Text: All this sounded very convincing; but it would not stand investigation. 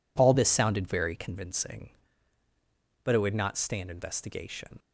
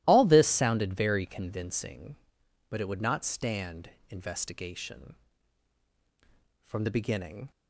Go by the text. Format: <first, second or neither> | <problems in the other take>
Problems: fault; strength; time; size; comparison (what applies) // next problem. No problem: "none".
first | starts louder than the rest; strong; until 1.0 s; 15 dB // pauses between "stand" and "investigation"; slight; at 3.8 s; 0.16 s long // goes on to say "From the beginning"; noticeable; from 6.6 s on; 0.84 s long